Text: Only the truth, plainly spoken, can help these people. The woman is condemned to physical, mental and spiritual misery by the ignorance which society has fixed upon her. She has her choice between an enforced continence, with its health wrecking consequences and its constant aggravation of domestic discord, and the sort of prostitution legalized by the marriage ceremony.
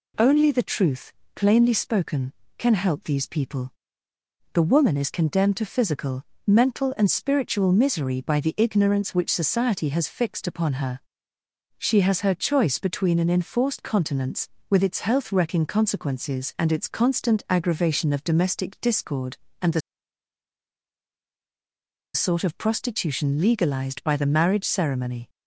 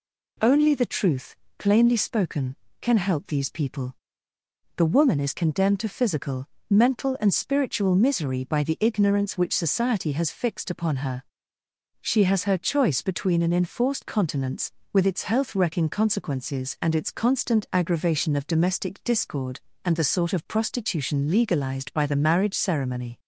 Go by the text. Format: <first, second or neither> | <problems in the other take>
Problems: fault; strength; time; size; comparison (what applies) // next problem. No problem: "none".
second | pauses between "the" and "sort"; strong; at 19.8 s; 2.3 s long